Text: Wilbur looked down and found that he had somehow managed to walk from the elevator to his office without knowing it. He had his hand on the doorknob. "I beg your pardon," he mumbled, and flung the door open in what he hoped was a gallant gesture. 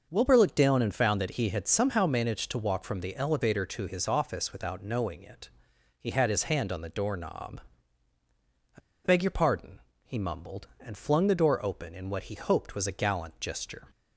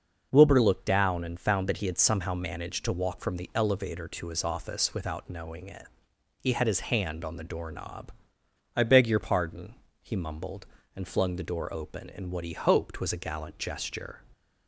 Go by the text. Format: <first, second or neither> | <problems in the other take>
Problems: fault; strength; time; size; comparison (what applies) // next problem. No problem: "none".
second | pauses between "I" and "beg"; slight; at 8.8 s; 0.23 s long